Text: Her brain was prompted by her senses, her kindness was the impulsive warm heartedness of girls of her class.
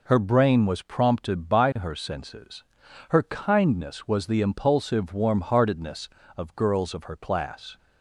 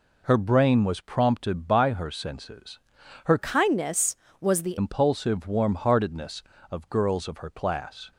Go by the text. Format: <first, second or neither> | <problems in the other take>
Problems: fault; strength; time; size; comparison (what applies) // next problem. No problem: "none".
first | changes voice from "kindness" to "the"; from 3.3 to 4.7 s; 1.4 s long